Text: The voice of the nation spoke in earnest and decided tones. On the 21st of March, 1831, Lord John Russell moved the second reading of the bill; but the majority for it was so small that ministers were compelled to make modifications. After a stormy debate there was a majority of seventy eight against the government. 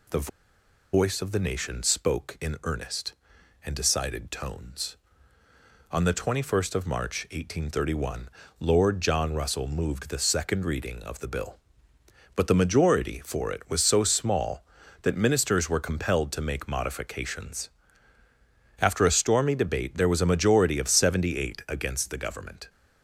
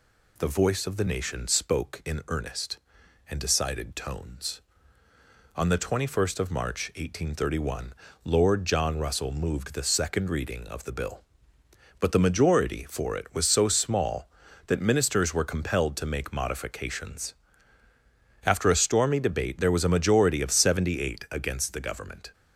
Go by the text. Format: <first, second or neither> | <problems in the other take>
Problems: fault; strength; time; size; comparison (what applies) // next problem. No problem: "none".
second | pauses between "The" and "voice"; noticeable; at 0.2 s; 0.65 s long